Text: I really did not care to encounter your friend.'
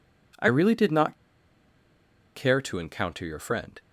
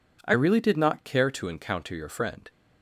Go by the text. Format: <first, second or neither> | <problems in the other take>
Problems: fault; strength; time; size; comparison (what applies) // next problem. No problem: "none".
second | pauses between "not" and "care"; at 1.1 s; 1.1 s long